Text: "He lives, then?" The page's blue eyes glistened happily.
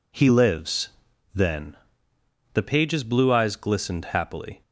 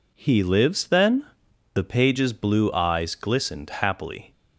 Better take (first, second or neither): neither